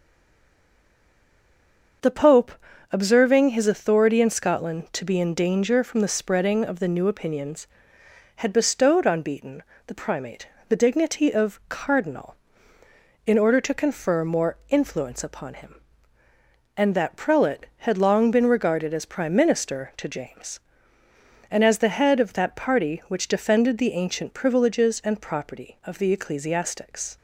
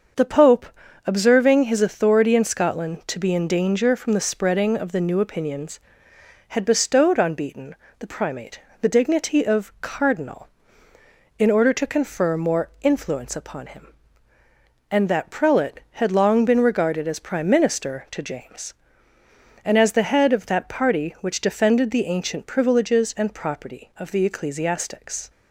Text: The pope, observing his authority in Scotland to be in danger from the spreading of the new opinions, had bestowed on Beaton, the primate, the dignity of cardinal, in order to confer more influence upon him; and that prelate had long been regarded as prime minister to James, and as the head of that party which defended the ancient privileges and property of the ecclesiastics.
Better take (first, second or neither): second